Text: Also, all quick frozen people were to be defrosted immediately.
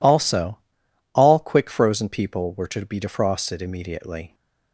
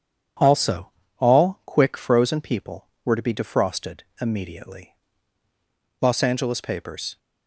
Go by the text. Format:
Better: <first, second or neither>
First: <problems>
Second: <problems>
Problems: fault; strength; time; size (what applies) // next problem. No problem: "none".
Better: first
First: none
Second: starts louder than the rest; strong; until 1.7 s; 8.5 dB // pauses between "defrosted" and "immediately"; slight; at 4.0 s; 0.20 s long // goes on to say "Los Angeles papers"; noticeable; from 5.9 s on; 1.1 s long